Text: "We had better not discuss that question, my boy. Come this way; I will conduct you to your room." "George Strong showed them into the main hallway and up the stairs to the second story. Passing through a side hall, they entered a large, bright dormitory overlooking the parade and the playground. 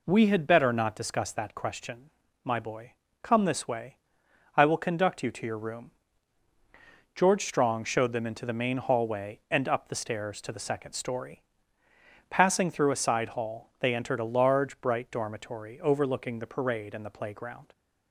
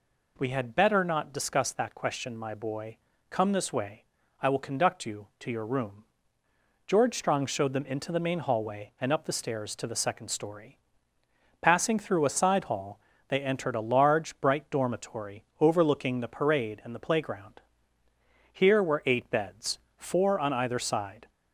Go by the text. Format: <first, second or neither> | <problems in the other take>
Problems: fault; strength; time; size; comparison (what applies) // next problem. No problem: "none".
first | pauses between "dormitory" and "overlooking"; slight; at 15.4 s; 0.16 s long // goes on to say "Here were eight beds four on either side"; strong; from 18.5 s on; 2.7 s long